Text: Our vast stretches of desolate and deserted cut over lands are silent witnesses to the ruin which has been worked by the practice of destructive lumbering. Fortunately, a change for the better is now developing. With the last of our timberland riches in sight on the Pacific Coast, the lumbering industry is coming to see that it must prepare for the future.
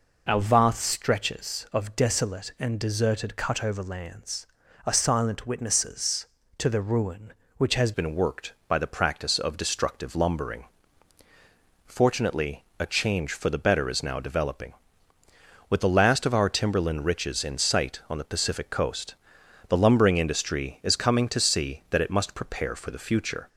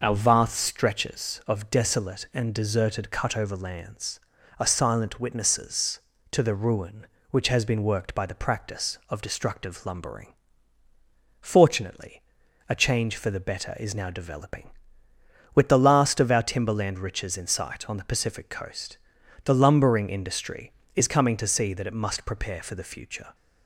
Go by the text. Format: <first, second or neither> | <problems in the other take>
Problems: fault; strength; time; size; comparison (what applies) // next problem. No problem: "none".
second | changes voice at "been"; from 7.9 s on; 15.5 s long